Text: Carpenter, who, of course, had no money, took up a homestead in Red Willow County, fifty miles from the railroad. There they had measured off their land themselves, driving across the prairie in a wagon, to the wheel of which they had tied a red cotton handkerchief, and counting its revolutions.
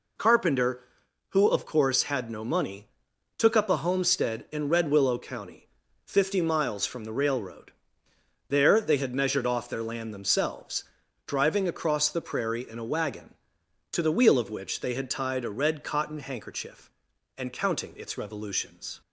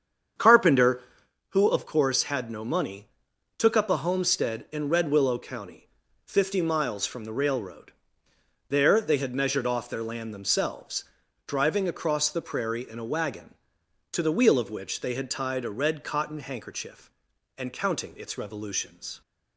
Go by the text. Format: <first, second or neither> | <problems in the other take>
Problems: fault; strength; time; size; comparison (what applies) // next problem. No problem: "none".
first | starts louder than the rest; strong; until 1.4 s; 8 dB